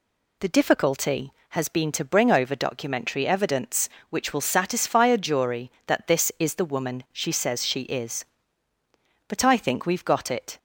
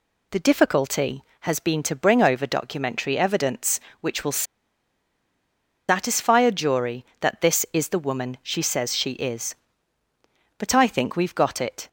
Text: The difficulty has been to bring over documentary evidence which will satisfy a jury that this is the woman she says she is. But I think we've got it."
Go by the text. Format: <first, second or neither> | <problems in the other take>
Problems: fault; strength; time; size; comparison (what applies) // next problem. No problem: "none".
first | pauses between "will" and "satisfy"; strong; at 4.4 s; 1.4 s long